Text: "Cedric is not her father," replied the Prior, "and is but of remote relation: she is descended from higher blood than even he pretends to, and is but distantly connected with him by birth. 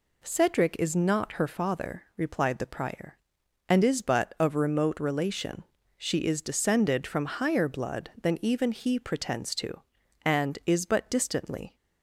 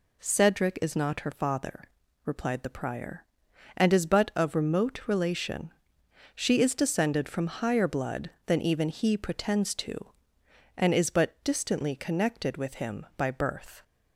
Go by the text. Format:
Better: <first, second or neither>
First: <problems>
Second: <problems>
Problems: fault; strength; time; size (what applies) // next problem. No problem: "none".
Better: second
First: stops before "connected with him by birth"; at 11.7 s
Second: none